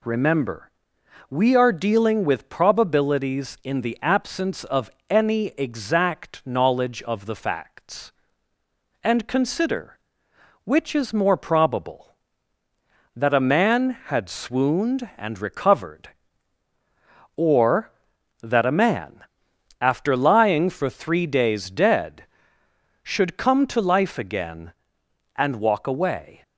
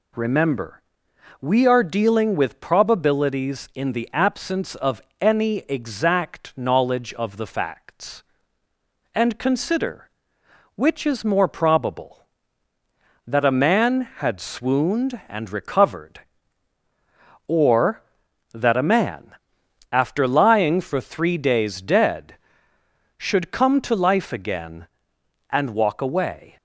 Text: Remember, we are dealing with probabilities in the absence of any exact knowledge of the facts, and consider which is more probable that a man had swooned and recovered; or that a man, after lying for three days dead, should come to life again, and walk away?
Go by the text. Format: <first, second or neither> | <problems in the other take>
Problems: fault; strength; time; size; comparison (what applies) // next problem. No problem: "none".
neither | pauses between "of" and "any"; slight; the same in both